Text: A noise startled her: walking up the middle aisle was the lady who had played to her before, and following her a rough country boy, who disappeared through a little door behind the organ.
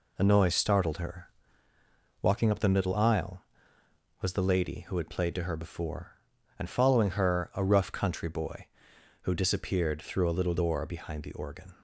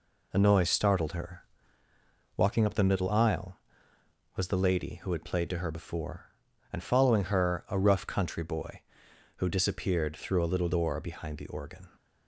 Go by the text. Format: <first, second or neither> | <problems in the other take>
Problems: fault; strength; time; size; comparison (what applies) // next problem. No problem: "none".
neither | none